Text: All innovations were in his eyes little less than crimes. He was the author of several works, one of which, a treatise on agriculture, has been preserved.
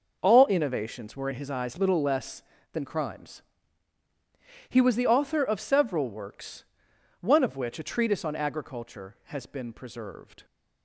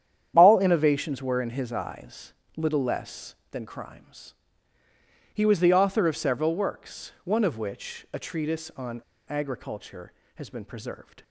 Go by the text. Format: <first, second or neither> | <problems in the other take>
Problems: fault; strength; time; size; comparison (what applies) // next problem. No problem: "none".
first | starts louder than the rest; strong; until 1.3 s; 9.5 dB // pauses between "eyes" and "little"; slight; at 2.3 s; 0.24 s long // pauses between "on" and "agriculture"; slight; at 9.0 s; 0.27 s long